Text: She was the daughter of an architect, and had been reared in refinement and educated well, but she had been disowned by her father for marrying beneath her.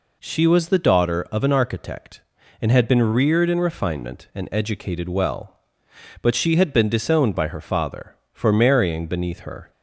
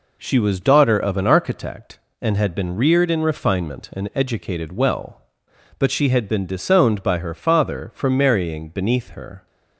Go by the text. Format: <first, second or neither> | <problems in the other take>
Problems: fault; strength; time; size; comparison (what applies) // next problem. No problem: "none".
first | skips "the"; at 0.6 s